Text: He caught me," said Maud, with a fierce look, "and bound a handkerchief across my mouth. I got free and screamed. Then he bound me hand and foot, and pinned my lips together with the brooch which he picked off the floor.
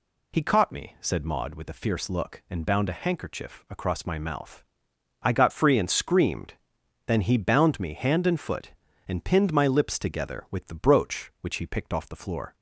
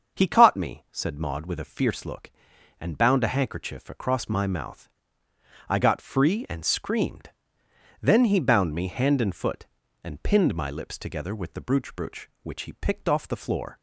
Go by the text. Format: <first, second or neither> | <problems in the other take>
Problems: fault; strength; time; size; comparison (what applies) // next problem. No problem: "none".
first | starts louder than the rest; until 1.2 s; 6.5 dB // says "brooch" twice; at 11.9 s